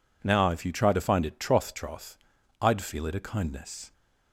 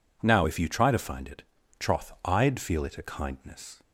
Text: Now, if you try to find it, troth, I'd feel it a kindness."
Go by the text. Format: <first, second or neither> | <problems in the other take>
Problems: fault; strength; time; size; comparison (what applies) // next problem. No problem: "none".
second | says "troth" twice; at 1.7 s